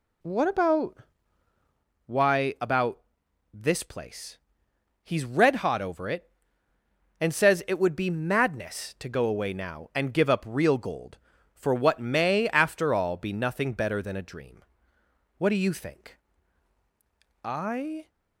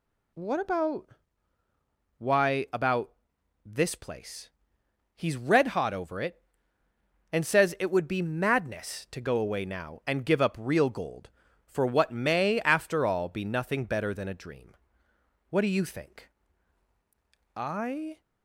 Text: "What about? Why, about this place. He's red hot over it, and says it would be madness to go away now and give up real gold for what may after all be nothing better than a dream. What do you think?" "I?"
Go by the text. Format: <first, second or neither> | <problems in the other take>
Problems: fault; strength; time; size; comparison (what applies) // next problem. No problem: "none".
second | starts louder than the rest; slight; until 1.9 s; 2.5 dB // pauses between "about" and "this"; noticeable; at 2.9 s; 0.54 s long; noticeable in the second